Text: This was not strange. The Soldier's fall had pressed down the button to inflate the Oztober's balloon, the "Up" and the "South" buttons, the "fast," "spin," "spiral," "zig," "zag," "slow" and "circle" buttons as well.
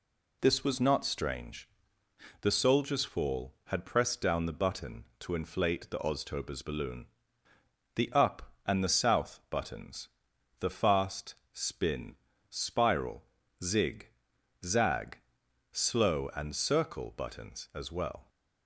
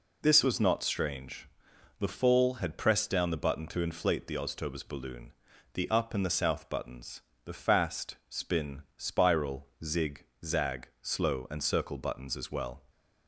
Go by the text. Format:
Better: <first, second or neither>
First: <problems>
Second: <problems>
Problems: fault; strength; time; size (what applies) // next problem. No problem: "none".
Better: first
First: none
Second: skips "Soldier's"; at 2.0 s